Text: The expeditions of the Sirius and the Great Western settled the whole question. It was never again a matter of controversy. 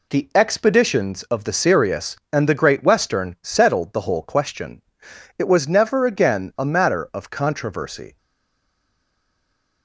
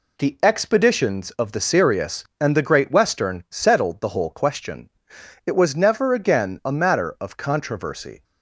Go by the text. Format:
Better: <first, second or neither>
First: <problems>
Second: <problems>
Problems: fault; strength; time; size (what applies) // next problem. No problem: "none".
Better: second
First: stays silent after the last word; noticeable; from 8.1 s on; 1.7 s long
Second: none